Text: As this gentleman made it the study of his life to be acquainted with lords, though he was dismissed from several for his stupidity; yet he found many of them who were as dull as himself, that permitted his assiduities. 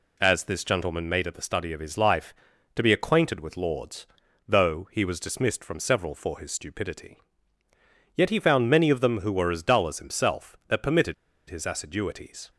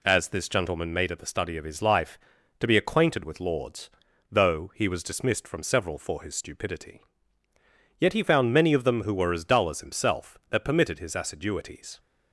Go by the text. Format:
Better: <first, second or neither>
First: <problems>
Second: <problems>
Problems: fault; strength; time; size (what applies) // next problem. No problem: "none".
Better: second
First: pauses between "permitted" and "his"; slight; at 11.1 s; 0.35 s long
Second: none